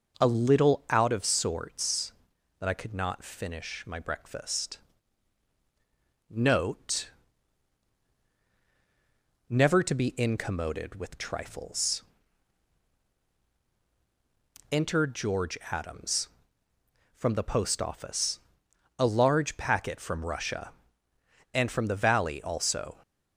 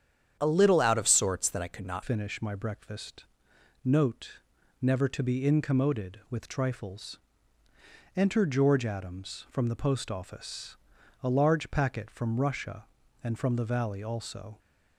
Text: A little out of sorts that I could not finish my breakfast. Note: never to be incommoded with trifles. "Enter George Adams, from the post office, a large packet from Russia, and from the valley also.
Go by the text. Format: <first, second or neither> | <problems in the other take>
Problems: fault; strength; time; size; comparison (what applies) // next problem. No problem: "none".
first | starts louder than the rest; strong; until 1.4 s; 9 dB // changes voice at "finish"; from 2.0 s on; 12.5 s long